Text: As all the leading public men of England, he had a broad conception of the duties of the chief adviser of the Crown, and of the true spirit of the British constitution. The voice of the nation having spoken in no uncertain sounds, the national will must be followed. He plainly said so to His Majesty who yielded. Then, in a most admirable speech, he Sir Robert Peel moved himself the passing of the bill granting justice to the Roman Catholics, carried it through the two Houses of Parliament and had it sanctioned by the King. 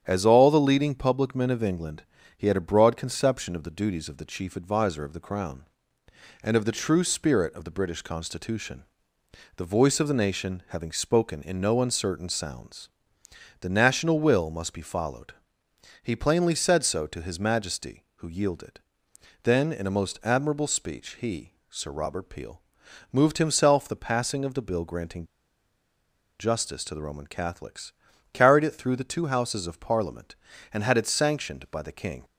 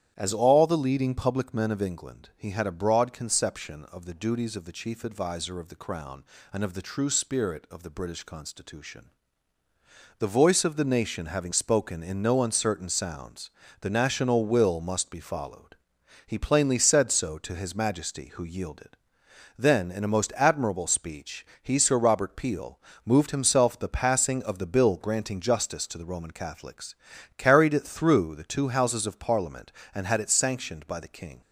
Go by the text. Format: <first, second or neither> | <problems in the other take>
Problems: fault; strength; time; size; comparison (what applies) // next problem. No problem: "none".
second | starts louder than the rest; strong; until 1.0 s; 9 dB; strong in the second // pauses between "he" and "Sir"; slight; at 21.5 s; 0.18 s long // pauses between "Peel" and "moved"; noticeable; at 22.5 s; 0.52 s long; slight in the second // pauses between "granting" and "justice"; at 25.2 s; 1.1 s long